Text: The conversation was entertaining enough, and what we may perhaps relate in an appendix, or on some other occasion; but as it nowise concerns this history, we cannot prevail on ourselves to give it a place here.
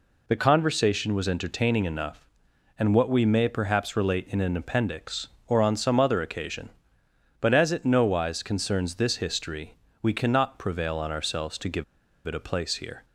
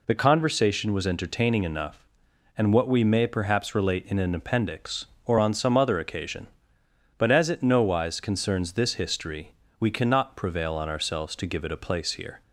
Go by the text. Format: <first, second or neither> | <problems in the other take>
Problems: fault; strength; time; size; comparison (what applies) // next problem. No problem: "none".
second | pauses between "give" and "it"; at 11.8 s; 0.42 s long